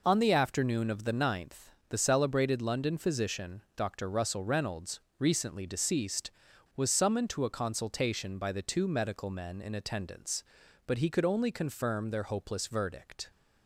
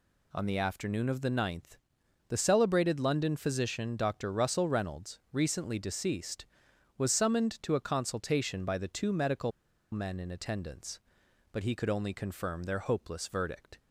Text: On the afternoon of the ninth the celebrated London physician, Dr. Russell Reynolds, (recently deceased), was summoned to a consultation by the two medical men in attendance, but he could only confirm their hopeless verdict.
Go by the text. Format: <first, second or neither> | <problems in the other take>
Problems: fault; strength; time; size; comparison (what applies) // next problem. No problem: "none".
first | pauses between "ninth" and "the"; noticeable; at 1.7 s; 0.52 s long; slight in the first // pauses between "medical" and "men"; at 9.5 s; 0.41 s long